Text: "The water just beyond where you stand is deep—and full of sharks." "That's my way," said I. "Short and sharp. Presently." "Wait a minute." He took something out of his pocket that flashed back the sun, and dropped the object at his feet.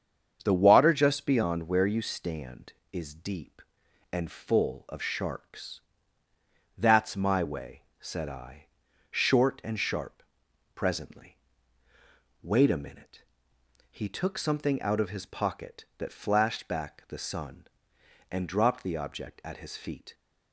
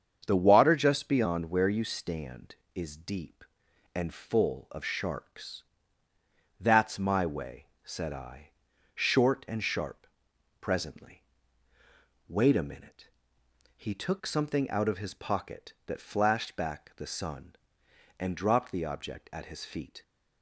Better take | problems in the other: neither | starts louder than the rest; strong; the same in both

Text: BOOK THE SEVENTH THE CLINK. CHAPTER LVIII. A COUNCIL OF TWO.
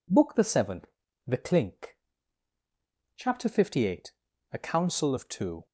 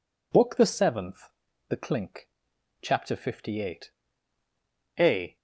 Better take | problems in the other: first | pauses between "SEVENTH" and "THE"; at 1.3 s; 0.38 s long; also in the first // stops before "COUNCIL OF TWO"; at 5.3 s

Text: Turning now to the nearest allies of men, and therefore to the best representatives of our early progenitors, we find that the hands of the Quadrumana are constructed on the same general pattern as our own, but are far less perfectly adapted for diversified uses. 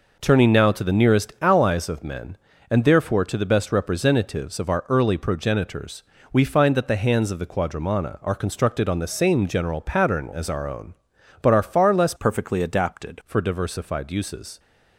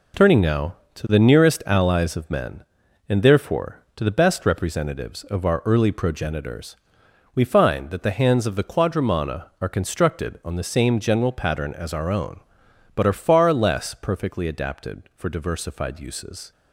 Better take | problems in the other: second | changes voice from "perfectly" to "adapted"; from 12.1 to 13.2 s; 1.1 s long

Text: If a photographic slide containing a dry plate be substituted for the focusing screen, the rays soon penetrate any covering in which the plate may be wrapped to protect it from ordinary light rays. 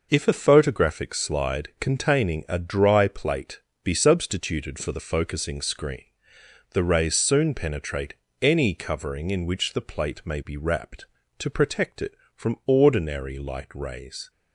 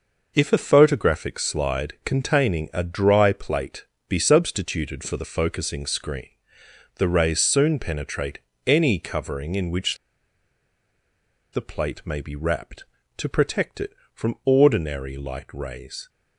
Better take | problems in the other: first | pauses between "plate" and "be"; slight; at 3.8 s; 0.24 s long; slight in the first // pauses between "penetrate" and "any"; slight; at 8.3 s; 0.26 s long; slight in the first // pauses between "which" and "the"; strong; at 9.9 s; 1.5 s long

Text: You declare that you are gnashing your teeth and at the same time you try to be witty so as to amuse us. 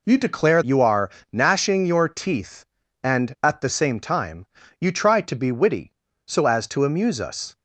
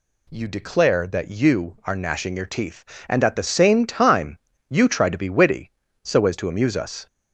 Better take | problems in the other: second | skips "that"; at 0.6 s // pauses between "are" and "gnashing"; slight; at 1.0 s; 0.22 s long // pauses between "time" and "you"; slight; at 4.4 s; 0.34 s long; slight in the second

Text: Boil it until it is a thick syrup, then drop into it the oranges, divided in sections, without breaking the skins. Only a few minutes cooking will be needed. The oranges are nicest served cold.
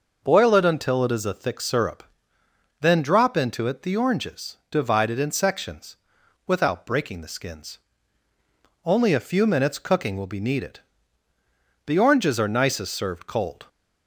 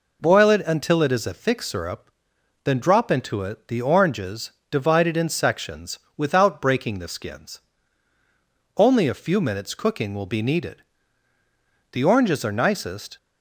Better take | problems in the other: first | stops before "served cold"; at 13.1 s

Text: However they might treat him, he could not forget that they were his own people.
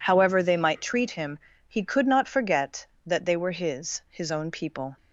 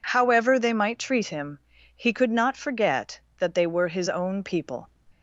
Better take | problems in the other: second | says "his" twice; at 4.0 s

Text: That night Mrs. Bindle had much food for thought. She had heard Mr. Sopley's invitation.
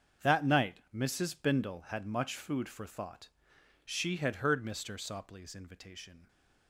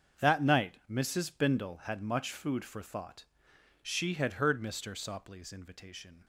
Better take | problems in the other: neither | starts louder than the rest; the same in both

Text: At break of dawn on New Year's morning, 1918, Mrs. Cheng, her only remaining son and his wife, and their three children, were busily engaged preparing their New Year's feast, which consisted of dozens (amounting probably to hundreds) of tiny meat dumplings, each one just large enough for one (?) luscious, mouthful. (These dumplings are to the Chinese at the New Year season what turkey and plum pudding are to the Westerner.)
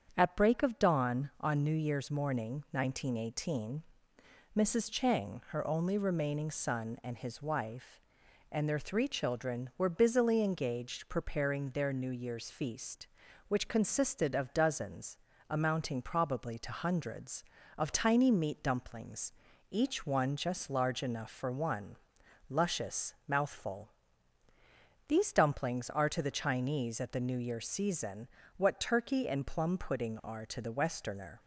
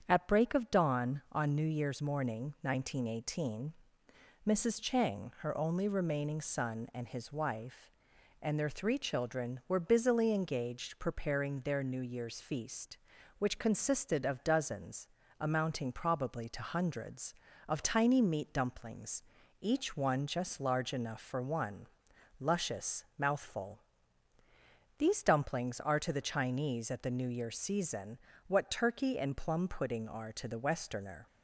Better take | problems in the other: neither | starts louder than the rest; strong; the same in both // pauses between "season" and "what"; slight; the same in both

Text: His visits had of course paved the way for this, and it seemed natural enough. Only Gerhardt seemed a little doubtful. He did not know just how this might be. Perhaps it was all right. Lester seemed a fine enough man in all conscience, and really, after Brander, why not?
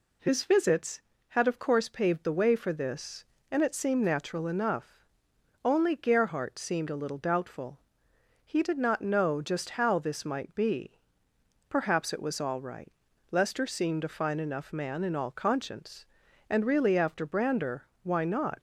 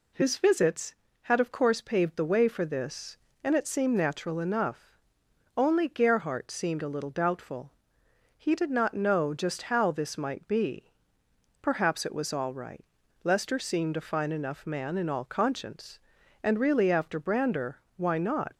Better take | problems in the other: neither | none

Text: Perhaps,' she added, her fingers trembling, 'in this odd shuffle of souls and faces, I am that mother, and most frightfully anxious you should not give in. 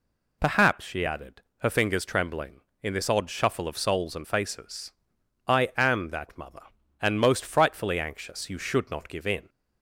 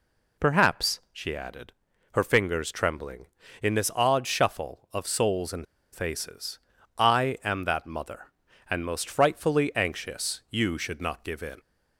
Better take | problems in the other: first | pauses between "and" and "faces"; slight; at 5.6 s; 0.28 s long

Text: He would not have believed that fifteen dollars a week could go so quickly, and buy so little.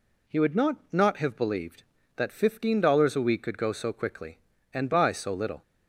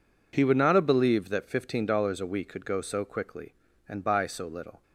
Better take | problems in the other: second | says "not" twice; at 0.9 s

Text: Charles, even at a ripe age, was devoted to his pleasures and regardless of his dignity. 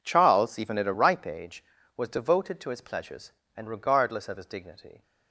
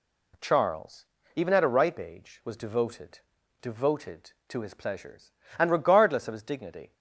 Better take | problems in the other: first | says "devoted" twice; at 3.6 s

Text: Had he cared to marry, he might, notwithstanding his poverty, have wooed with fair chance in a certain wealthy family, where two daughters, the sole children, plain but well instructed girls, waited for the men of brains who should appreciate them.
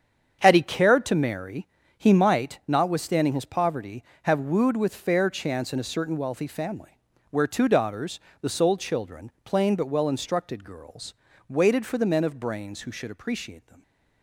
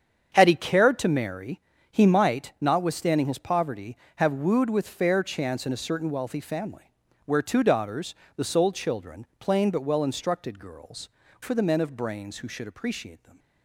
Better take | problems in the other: first | starts louder than the rest; strong; until 1.3 s; 7.5 dB; strong in the first // skips "waited"; at 11.2 s

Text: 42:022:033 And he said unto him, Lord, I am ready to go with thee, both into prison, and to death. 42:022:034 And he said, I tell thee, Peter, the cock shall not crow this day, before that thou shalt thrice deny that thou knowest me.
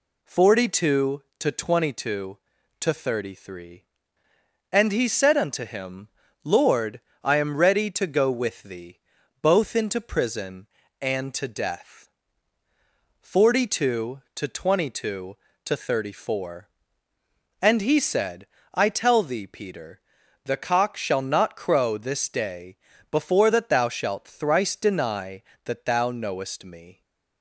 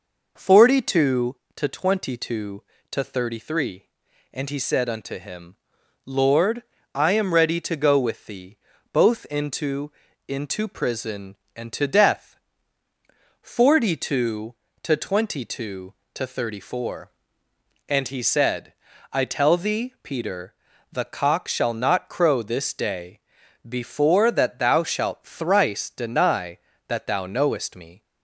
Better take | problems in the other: first | says "into" twice; at 10.2 s

